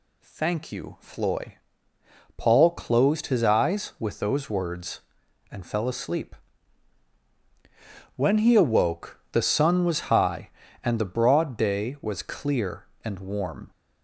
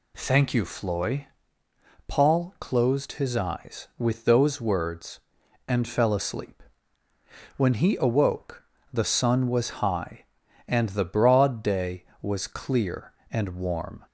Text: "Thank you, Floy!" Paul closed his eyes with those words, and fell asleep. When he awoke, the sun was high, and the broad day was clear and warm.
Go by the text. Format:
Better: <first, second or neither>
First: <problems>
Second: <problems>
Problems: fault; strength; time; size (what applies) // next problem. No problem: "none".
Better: neither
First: none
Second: none